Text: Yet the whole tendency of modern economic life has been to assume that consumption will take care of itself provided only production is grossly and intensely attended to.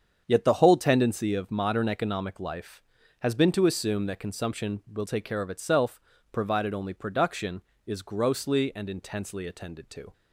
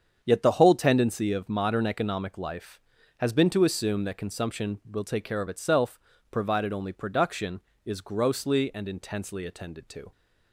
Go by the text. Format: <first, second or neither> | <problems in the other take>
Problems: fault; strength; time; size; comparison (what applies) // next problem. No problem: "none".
neither | starts louder than the rest; strong; the same in both // pauses between "itself" and "provided"; slight; the same in both